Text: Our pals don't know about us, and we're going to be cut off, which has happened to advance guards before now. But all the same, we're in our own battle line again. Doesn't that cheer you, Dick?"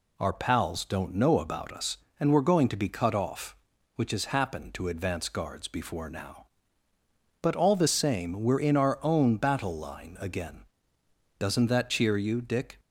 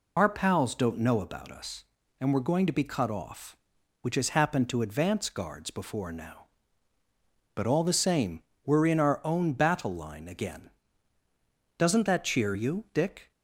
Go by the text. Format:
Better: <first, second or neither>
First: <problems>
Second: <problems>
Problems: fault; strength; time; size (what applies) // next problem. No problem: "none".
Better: first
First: none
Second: loses the start of "Our"; at 0.1 s; 50 ms